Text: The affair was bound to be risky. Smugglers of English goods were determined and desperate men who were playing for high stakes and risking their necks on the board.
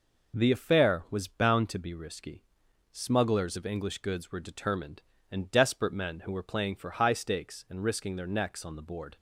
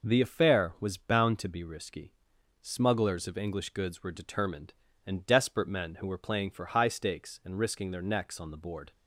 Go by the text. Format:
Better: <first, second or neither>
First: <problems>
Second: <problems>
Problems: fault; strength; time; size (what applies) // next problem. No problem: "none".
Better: neither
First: none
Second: none